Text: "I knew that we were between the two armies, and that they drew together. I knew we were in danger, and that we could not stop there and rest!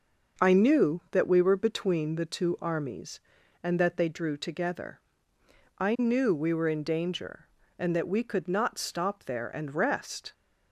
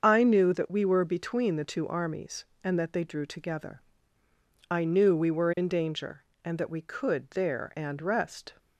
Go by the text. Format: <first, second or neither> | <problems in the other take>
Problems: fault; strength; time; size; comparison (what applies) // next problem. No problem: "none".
first | starts louder than the rest; until 1.0 s; 7 dB // skips "not stop"; at 7.2 s